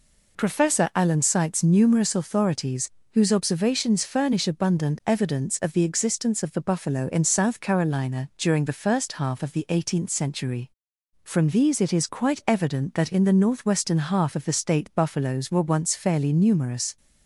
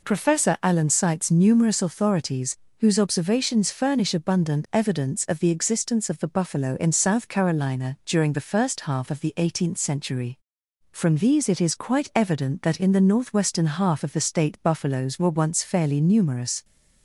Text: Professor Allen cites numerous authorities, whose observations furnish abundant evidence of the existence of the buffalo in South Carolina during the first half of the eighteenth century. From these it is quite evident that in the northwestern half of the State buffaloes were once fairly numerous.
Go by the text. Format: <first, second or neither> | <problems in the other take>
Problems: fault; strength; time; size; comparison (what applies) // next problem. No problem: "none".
neither | none